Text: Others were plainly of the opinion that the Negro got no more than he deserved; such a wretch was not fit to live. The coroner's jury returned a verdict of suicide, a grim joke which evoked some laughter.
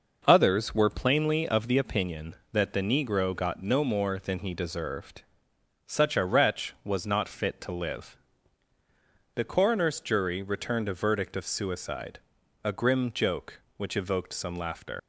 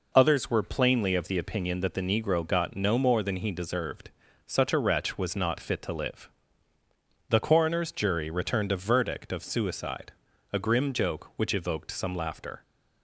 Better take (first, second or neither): second